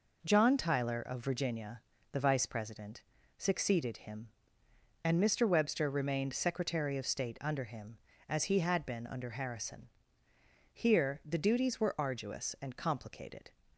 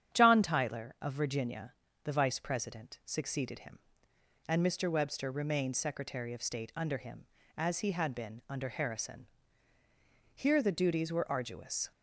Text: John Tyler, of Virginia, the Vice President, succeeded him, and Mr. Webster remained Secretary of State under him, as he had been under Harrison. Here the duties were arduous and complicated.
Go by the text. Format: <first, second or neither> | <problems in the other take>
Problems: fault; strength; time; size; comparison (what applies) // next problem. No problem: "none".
first | starts louder than the rest; strong; until 1.2 s; 9 dB // stops before "and complicated"; at 11.9 s